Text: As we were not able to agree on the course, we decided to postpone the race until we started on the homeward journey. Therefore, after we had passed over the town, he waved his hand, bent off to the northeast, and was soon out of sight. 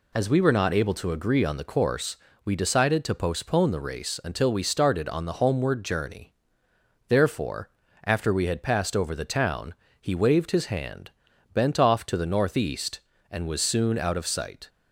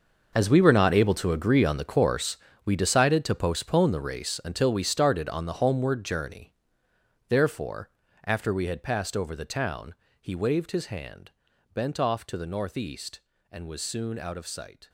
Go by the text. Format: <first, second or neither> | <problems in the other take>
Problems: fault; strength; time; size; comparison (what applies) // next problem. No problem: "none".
first | gets quieter; strong; throughout; 14.5 dB